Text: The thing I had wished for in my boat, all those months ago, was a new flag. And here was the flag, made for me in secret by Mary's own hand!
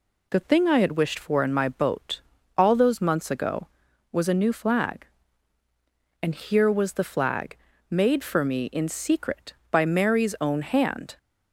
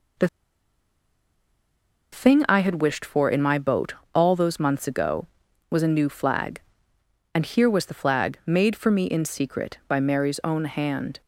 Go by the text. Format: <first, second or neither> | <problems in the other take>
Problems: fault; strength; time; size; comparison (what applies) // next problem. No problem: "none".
first | pauses between "The" and "thing"; strong; at 0.2 s; 1.8 s long